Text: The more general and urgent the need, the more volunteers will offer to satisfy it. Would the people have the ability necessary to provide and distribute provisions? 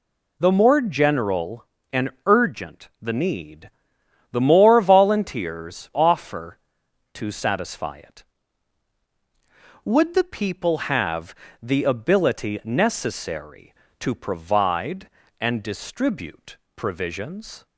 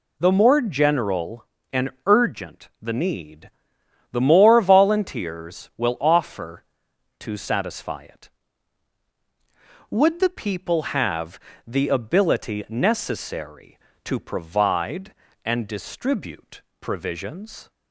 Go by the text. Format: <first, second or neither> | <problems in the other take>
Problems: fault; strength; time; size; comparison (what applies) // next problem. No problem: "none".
second | pauses between "and" and "urgent"; slight; at 2.0 s; 0.16 s long; slight in the second // skips "will"; at 5.9 s // pauses between "have" and "the"; slight; at 11.3 s; 0.28 s long; slight in the second // pauses between "distribute" and "provisions"; slight; at 16.5 s; 0.18 s long; slight in the second